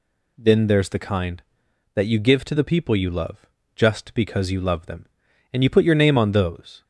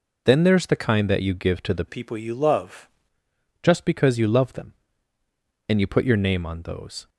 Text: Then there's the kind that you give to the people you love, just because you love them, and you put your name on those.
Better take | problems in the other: first | changes voice from "people" to "love"; from 1.8 to 2.8 s; 1.0 s long

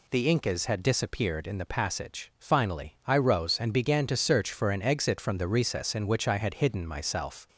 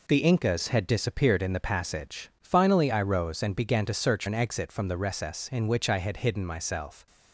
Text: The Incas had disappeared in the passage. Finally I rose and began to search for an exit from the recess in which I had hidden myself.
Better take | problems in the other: first | skips "for"; at 4.2 s

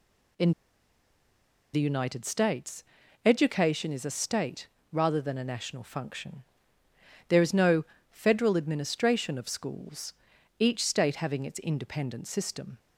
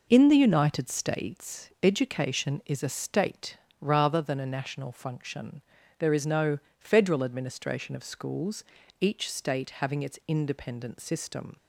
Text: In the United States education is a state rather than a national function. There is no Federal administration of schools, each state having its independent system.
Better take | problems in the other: second | pauses between "In" and "the"; at 0.5 s; 1.2 s long // pauses between "States" and "education"; at 2.8 s; 0.42 s long // pauses between "state" and "rather"; slight; at 4.6 s; 0.24 s long; slight in the second // pauses between "no" and "Federal"; slight; at 7.8 s; 0.26 s long; slight in the second

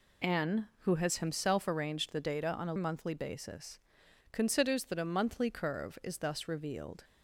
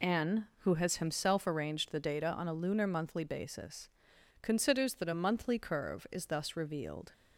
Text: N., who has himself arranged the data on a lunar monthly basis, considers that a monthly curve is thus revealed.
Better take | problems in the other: second | skips "lunar"; at 2.7 s

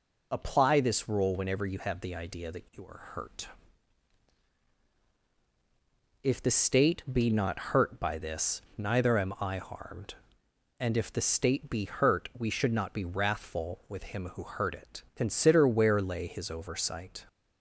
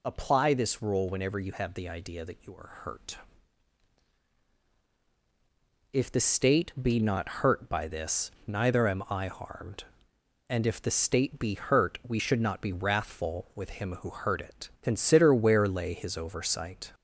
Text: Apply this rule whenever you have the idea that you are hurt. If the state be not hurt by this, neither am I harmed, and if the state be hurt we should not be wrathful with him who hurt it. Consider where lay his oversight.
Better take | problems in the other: first | gets louder; slight; throughout; 2 dB

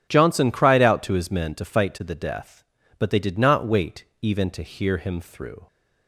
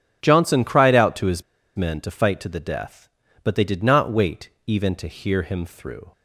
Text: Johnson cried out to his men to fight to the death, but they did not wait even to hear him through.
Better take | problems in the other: first | pauses between "his" and "men"; slight; at 1.4 s; 0.33 s long // pauses between "wait" and "even"; slight; at 4.4 s; 0.16 s long; slight in the first

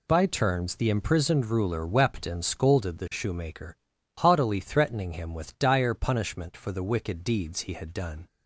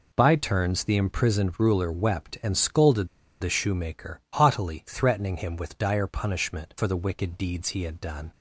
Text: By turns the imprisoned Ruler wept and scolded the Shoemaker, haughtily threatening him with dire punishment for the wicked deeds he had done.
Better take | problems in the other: first | pauses between "scolded" and "the"; slight; at 3.0 s; 0.33 s long

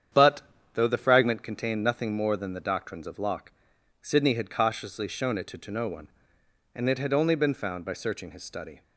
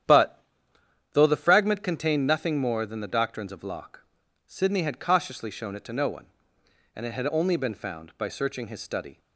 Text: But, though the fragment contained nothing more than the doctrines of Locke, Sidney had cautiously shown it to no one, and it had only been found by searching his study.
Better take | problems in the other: second | starts louder than the rest; strong; until 1.4 s; 8.5 dB; strong in the second // says "to" twice; at 5.5 s

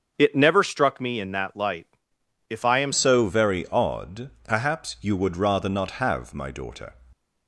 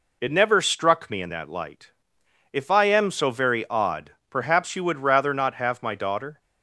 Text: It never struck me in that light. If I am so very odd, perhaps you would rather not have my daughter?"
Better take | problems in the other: second | starts louder than the rest; until 1.1 s; 7 dB // changes voice at "so"; from 2.9 s on; 4.0 s long

